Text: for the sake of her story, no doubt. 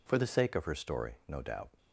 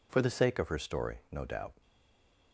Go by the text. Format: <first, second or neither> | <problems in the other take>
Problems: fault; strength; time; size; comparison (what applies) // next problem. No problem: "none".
first | stays silent after the last word; slight; from 1.8 s on; 0.7 s long